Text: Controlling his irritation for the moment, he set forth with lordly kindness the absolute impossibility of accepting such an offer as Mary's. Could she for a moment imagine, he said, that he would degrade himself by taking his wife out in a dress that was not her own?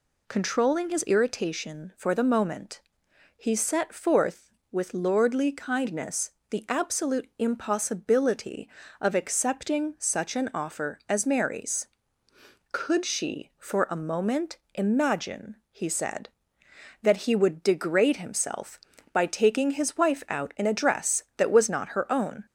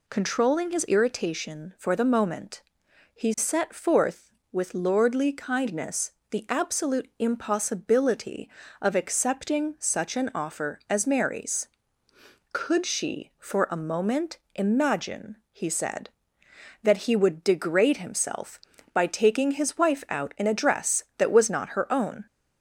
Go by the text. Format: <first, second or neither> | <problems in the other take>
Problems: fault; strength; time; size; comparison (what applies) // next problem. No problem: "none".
neither | pauses between "kindness" and "the"; slight; the same in both // pauses between "moment" and "imagine"; slight; the same in both